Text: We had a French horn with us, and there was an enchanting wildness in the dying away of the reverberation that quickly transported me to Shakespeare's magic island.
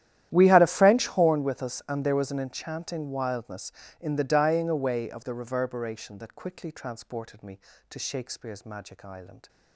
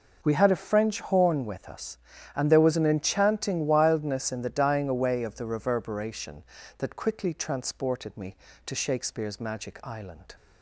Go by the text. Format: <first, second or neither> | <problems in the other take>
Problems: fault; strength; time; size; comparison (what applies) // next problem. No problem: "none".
second | starts louder than the rest; strong; until 1.4 s; 12 dB